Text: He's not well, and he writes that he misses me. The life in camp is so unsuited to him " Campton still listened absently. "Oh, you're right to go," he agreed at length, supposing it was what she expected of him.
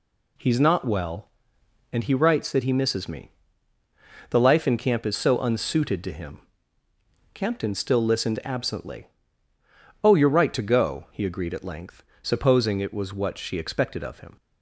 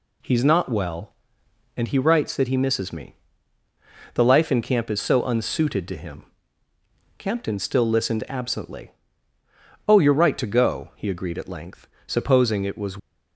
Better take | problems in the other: first | stops before "what she expected of him"; at 12.9 s

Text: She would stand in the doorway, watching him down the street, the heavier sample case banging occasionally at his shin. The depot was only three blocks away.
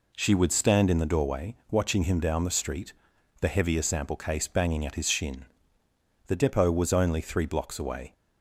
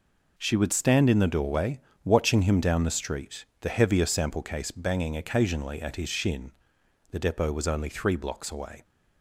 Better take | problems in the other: second | skips "occasionally"; at 4.8 s

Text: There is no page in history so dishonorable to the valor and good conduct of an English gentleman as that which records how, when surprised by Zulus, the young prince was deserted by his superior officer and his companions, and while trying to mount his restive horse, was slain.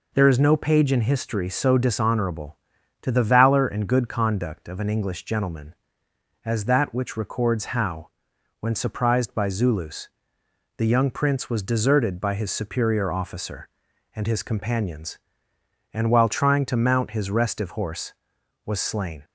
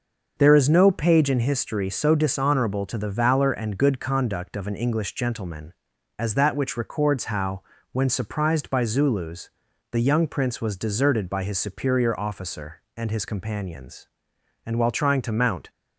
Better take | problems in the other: first | starts louder than the rest; noticeable; until 1.3 s; 6 dB // stops before "his restive horse was slain"; at 15.6 s

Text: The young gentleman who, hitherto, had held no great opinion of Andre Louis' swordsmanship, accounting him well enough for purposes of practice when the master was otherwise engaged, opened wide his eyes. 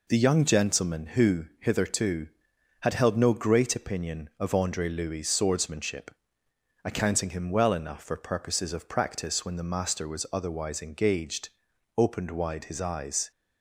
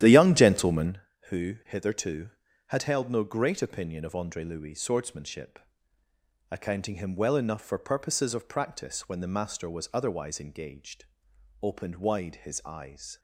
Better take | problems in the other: first | starts louder than the rest; strong; until 1.0 s; 11.5 dB

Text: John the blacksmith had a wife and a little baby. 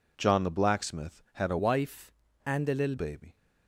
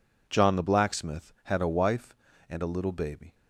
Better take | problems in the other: second | changes voice from "wife" to "little"; from 1.5 to 2.9 s; 1.4 s long

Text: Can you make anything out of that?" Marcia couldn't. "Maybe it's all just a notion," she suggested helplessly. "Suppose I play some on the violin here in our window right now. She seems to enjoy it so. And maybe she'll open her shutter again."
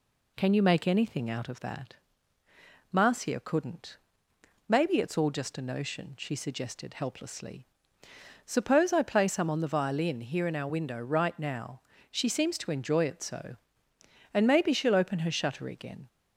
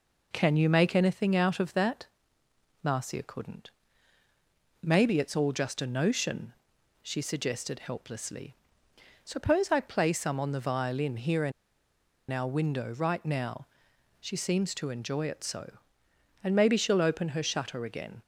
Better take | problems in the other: first | pauses between "in" and "our"; noticeable; at 11.5 s; 0.79 s long

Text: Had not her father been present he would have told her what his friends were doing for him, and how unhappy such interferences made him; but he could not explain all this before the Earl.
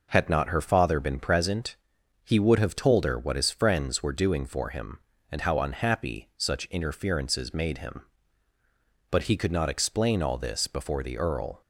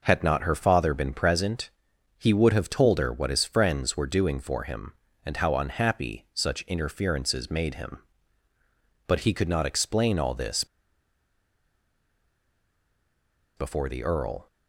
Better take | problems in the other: first | pauses between "present" and "he"; noticeable; at 1.6 s; 0.48 s long; noticeable in the first // pauses between "this" and "before"; strong; at 10.6 s; 2.9 s long

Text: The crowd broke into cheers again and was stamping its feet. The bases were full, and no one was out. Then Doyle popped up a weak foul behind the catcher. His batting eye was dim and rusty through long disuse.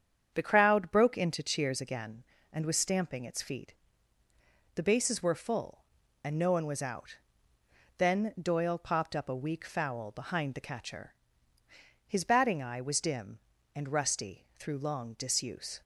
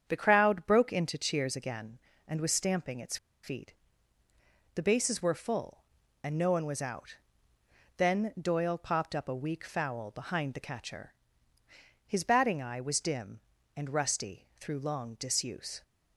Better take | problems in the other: first | starts louder than the rest; strong; until 1.0 s; 8 dB; strong in the first // pauses between "its" and "feet"; slight; at 3.1 s; 0.27 s long

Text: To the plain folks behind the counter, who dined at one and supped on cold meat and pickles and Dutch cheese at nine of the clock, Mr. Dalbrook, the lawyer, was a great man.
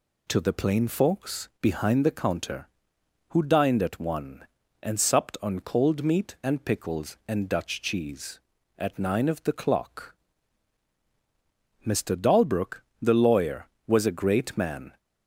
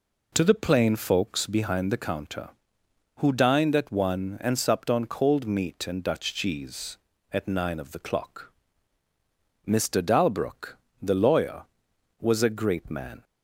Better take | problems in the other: first | skips "pickles and"; at 6.0 s

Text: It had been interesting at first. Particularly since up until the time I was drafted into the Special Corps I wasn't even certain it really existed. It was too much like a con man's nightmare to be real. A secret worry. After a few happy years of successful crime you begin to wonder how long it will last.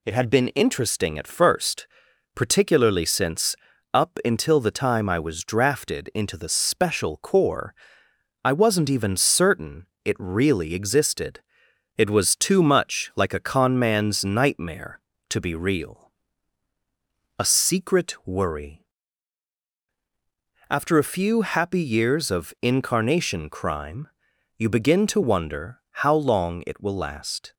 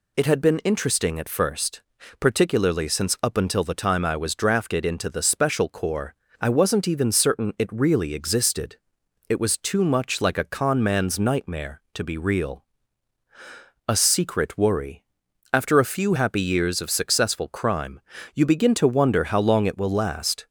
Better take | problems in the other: second | pauses between "since" and "up"; at 3.5 s; 0.38 s long // pauses between "Corps" and "I"; noticeable; at 7.7 s; 0.70 s long; slight in the second // pauses between "certain" and "it"; slight; at 9.8 s; 0.18 s long // says "incarnation" for "successful"; at 22.6 s // pauses between "crime" and "you"; noticeable; at 24.0 s; 0.50 s long; slight in the second

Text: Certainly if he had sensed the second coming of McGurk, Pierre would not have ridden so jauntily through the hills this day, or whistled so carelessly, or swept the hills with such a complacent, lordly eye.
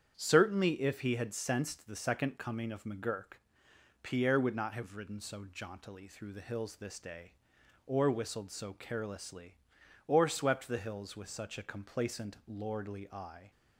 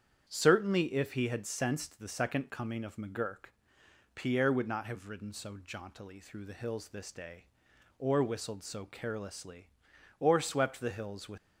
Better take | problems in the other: first | starts louder than the rest; strong; until 1.2 s; 8.5 dB; strong in the first // stops before "such a complacent lordly eye"; at 11.3 s

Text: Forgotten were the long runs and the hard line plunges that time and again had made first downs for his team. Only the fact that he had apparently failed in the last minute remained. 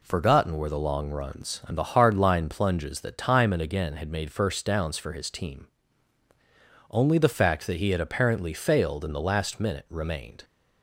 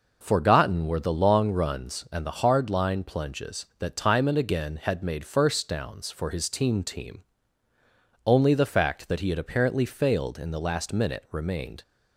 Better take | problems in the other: first | says "team" twice; at 6.8 s

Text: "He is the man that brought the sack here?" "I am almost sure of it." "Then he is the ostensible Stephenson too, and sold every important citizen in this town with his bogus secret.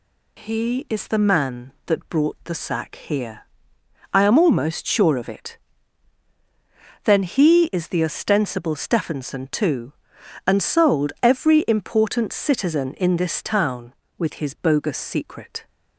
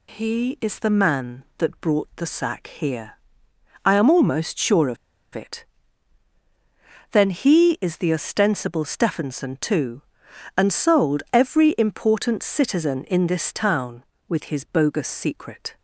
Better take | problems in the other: first | pauses between "of" and "it"; at 4.9 s; 0.38 s long

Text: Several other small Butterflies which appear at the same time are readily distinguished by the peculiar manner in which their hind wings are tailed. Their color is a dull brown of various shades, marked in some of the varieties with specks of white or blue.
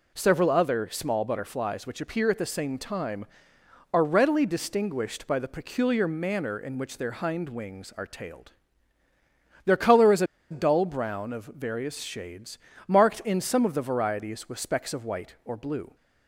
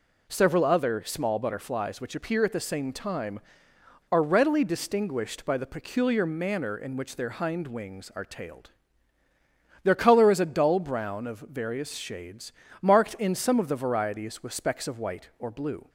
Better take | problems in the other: second | pauses between "a" and "dull"; slight; at 10.2 s; 0.24 s long

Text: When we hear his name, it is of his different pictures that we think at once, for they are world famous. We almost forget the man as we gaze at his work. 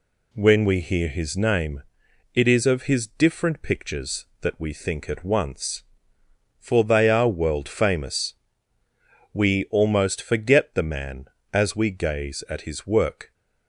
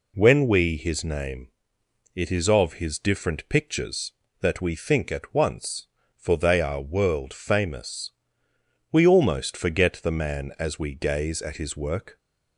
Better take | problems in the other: first | skips "hear"; at 0.7 s

